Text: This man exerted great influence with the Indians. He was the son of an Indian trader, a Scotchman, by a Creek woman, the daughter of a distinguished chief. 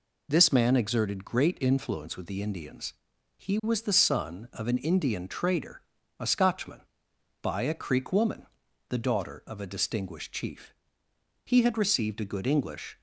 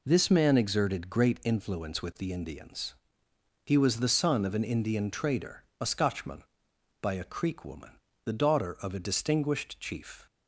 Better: second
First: goes on to say "He had received a good English"; from 11.4 s on; 1.5 s long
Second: none

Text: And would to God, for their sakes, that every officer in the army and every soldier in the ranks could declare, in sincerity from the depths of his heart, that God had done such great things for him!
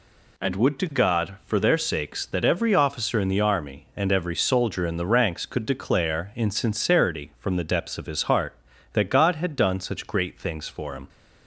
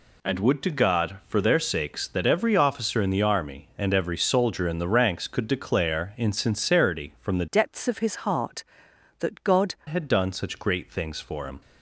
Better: first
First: none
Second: changes voice from "depths" to "God"; from 7.4 to 9.7 s; 2.3 s long

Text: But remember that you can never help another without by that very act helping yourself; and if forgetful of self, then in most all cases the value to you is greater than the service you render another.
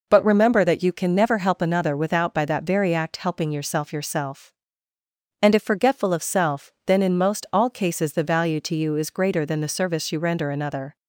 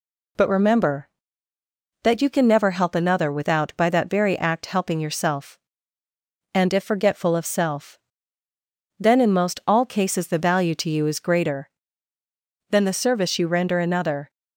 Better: second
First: says "yourself" twice; at 3.9 s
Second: none

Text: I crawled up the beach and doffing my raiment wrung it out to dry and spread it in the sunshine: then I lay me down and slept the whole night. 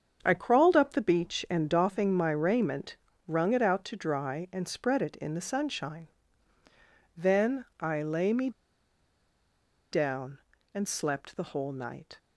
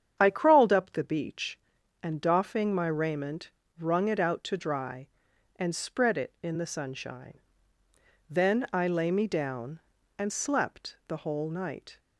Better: second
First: starts louder than the rest; strong; until 1.2 s; 7 dB // pauses between "raiment" and "wrung"; slight; at 2.9 s; 0.32 s long // pauses between "me" and "down"; strong; at 8.5 s; 1.4 s long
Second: starts louder than the rest; strong; until 1.2 s; 8.5 dB // pauses between "raiment" and "wrung"; slight; at 3.5 s; 0.28 s long

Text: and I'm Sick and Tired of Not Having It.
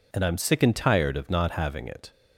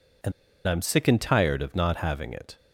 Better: first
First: none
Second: pauses between "and" and "I'm"; slight; at 0.3 s; 0.36 s long

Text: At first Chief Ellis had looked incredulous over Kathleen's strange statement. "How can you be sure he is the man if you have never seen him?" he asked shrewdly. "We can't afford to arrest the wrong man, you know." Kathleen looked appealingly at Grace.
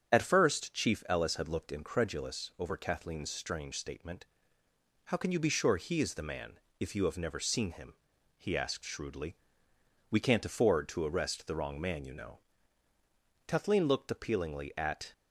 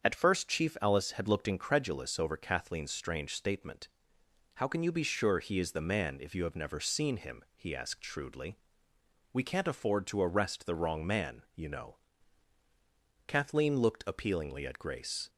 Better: second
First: starts louder than the rest; strong; until 1.1 s; 7.5 dB // pauses between "man" and "if"; slight; at 6.5 s; 0.22 s long // stops before "Grace"; at 15.1 s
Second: starts louder than the rest; until 1.0 s; 7 dB

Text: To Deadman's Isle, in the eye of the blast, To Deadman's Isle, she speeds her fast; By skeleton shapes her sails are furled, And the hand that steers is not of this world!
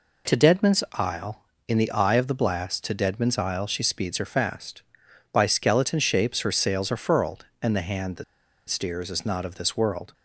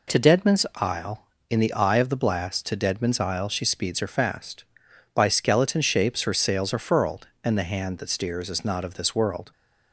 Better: second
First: pauses between "that" and "steers"; at 8.2 s; 0.44 s long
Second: none

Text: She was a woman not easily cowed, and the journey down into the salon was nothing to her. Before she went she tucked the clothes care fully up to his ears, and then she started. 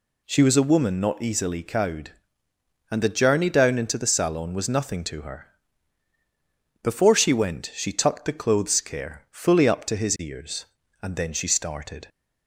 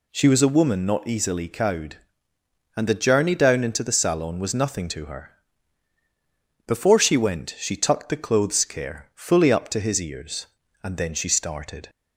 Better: neither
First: none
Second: none

